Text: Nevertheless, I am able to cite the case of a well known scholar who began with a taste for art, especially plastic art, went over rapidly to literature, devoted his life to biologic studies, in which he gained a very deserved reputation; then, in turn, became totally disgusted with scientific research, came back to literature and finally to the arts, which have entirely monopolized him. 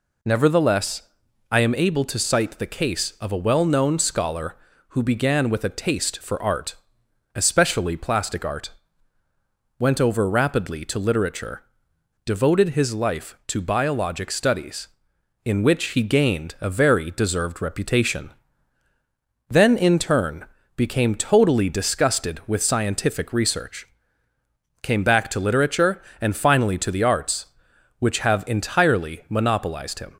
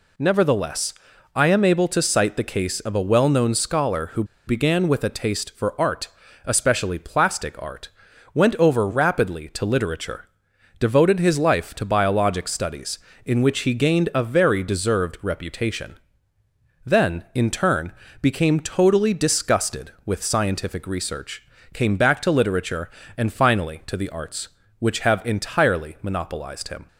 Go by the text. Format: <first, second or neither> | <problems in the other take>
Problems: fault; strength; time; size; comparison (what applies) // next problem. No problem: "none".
first | pauses between "who" and "began"; slight; at 4.2 s; 0.23 s long